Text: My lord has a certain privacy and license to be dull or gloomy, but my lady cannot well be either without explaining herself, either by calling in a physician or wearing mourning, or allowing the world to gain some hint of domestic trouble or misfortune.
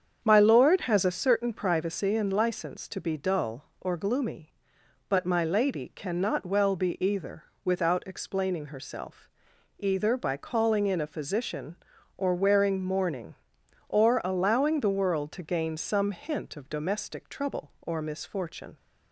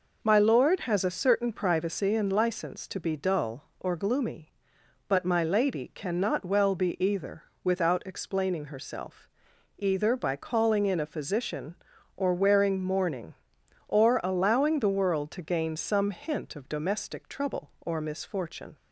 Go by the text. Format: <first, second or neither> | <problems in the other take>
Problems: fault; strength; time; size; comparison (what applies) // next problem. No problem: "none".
second | starts louder than the rest; strong; until 1.2 s; 7.5 dB // pauses between "either" and "without"; slight; at 7.4 s; 0.20 s long; slight in the second